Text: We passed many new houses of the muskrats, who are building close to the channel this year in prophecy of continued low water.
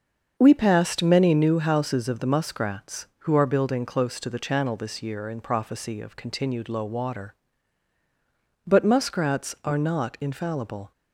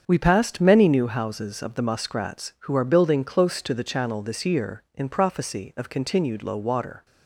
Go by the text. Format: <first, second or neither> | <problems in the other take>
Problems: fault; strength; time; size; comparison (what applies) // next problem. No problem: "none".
second | starts louder than the rest; until 1.3 s; 6.5 dB; strong in the second // goes on to say "But muskrats are not infallible"; strong; from 8.6 s on; 2.2 s long